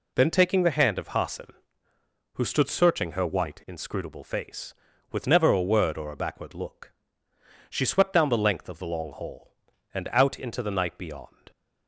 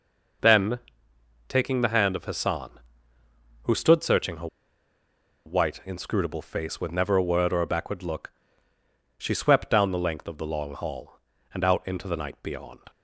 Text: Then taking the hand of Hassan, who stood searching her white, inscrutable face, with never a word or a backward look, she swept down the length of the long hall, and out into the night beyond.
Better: first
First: none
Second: pauses between "Then" and "taking"; noticeable; at 0.7 s; 0.68 s long // pauses between "her" and "white"; at 4.4 s; 0.98 s long

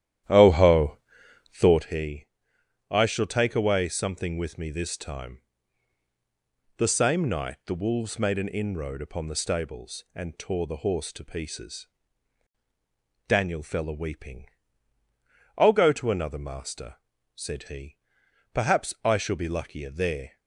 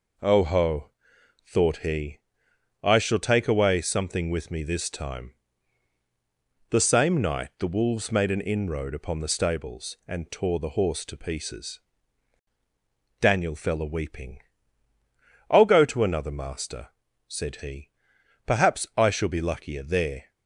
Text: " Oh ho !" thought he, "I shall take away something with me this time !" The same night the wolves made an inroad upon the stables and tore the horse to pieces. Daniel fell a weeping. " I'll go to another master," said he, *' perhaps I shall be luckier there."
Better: second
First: starts louder than the rest; strong; until 1.9 s; 11.5 dB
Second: none

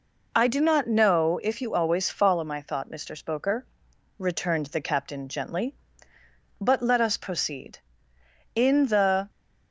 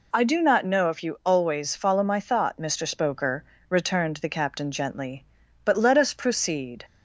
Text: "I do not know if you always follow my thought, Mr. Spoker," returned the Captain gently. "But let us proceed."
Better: second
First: goes on to say "In the"; noticeable; from 8.5 s on; 0.74 s long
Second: none

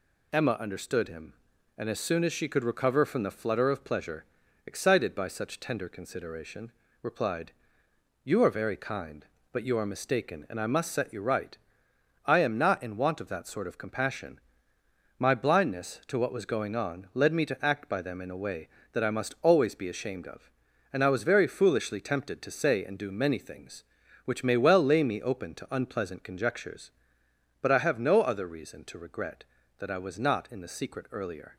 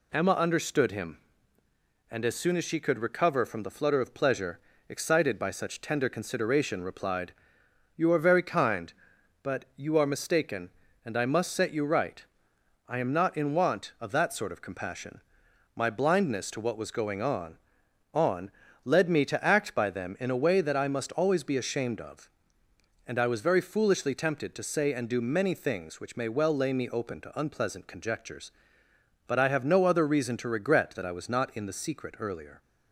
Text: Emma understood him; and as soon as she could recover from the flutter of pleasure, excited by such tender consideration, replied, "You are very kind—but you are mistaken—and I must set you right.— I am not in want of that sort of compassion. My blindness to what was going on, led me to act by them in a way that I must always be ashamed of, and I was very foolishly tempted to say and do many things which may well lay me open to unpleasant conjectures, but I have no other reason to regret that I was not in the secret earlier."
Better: first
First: none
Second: says "on" twice; at 18.1 s

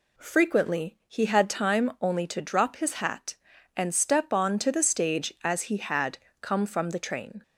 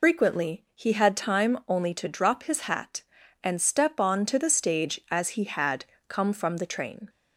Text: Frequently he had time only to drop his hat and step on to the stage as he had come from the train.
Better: first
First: pauses between "had" and "come"; slight; at 6.1 s; 0.22 s long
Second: loses the start of "Frequently"; at 0.0 s; 175 ms // pauses between "had" and "come"; slight; at 5.8 s; 0.22 s long

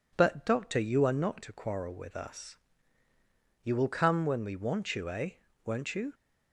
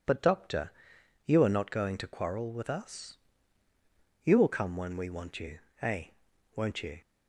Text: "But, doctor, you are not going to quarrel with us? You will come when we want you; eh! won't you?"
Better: second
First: skips "going"; at 1.4 s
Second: none

